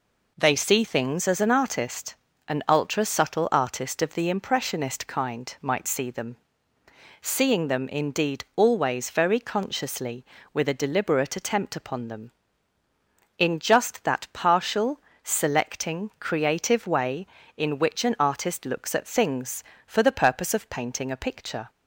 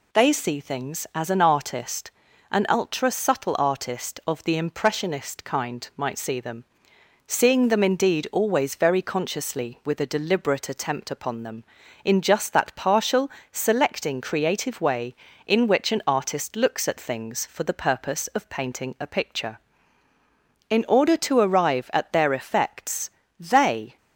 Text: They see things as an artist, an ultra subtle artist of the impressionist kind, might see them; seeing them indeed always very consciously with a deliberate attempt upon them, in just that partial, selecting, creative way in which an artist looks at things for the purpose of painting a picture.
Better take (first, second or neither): first